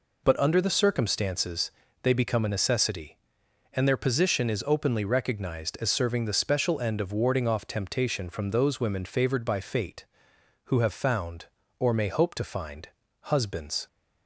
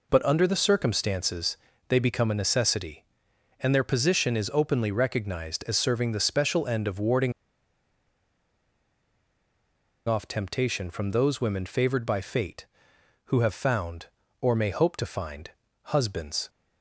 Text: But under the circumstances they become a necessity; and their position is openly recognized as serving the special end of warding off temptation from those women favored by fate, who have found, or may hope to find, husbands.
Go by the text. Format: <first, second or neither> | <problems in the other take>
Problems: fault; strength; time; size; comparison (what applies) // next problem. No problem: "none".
first | pauses between "circumstances" and "they"; slight; at 1.5 s; 0.32 s long; slight in the first // pauses between "warding" and "off"; strong; at 7.3 s; 2.7 s long